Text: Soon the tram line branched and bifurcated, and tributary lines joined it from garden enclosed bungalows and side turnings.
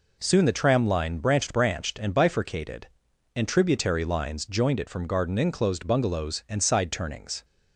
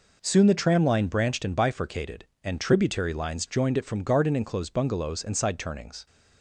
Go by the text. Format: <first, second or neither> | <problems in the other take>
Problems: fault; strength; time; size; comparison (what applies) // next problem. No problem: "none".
second | says "branched" twice; at 1.5 s